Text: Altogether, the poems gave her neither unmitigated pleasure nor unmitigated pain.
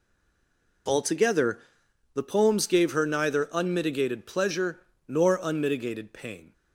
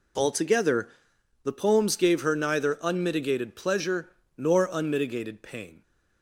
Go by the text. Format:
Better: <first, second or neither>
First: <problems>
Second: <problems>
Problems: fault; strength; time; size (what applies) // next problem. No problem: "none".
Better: second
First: stays silent before the first word; slight; until 0.8 s; 0.8 s long // pauses between "pleasure" and "nor"; slight; at 4.7 s; 0.30 s long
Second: pauses between "pleasure" and "nor"; slight; at 4.0 s; 0.30 s long